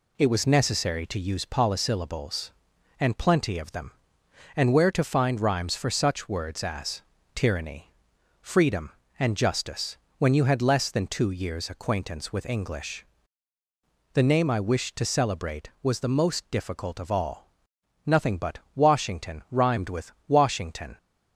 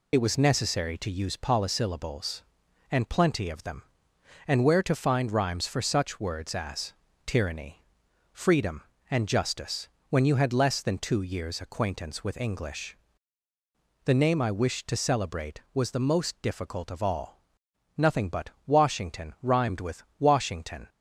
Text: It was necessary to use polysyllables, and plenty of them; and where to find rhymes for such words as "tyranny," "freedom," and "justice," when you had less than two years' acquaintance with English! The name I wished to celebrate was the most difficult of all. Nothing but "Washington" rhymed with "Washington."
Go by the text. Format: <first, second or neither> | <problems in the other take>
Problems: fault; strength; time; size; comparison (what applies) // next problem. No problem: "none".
first | loses the start of "It"; at 0.1 s; 45 ms // pauses between "as" and "tyranny"; slight; at 6.9 s; 0.32 s long; slight in the first // pauses between "but" and "Washington"; slight; at 18.5 s; 0.16 s long; slight in the first // pauses between "with" and "Washington"; slight; at 20.0 s; 0.16 s long; slight in the first